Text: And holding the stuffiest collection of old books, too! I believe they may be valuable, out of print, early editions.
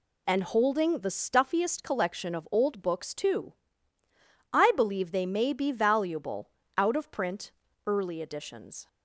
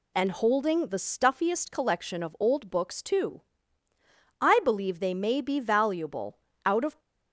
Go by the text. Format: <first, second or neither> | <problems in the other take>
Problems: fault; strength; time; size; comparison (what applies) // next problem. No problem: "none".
first | stops before "print early editions"; at 6.9 s